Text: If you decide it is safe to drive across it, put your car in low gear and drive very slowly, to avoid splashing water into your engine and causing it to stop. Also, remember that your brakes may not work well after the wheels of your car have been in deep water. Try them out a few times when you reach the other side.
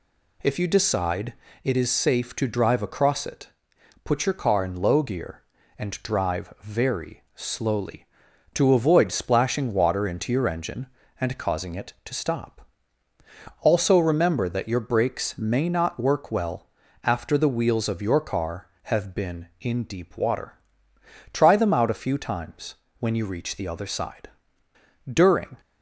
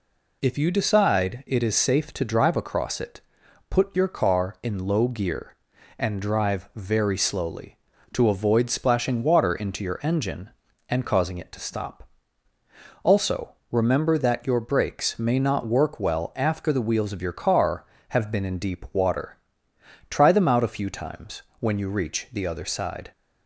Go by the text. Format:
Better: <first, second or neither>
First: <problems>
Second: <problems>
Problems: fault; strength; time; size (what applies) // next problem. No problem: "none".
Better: second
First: pauses between "decide" and "it"; slight; at 1.3 s; 0.30 s long // pauses between "well" and "after"; slight; at 16.6 s; 0.36 s long // pauses between "times" and "when"; slight; at 22.7 s; 0.24 s long // goes on to say "DURING"; from 25.0 s on; 0.50 s long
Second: pauses between "times" and "when"; slight; at 21.4 s; 0.16 s long